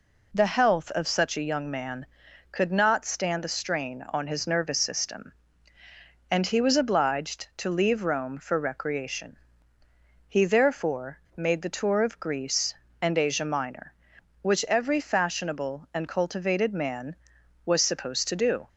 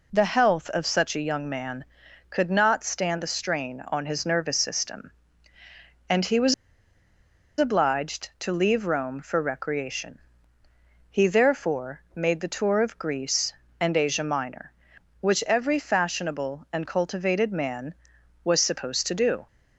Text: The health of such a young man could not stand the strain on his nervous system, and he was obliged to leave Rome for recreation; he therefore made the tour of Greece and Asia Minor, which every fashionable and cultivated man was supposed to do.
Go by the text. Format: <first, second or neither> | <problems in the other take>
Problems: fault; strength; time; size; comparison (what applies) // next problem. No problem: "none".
first | pauses between "was" and "obliged"; at 6.5 s; 1.0 s long // pauses between "therefore" and "made"; slight; at 12.0 s; 0.16 s long; slight in the first